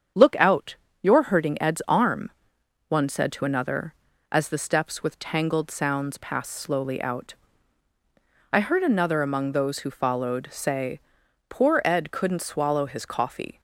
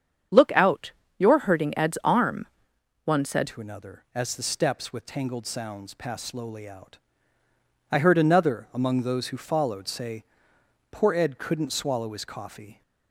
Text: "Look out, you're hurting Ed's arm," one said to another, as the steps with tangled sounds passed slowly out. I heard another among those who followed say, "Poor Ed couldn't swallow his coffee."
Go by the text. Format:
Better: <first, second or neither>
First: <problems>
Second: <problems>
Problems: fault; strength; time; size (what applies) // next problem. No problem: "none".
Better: first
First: starts louder than the rest; strong; until 1.4 s; 8 dB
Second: starts louder than the rest; strong; until 1.6 s; 8.5 dB // changes voice at "to"; from 3.4 s on; 9.4 s long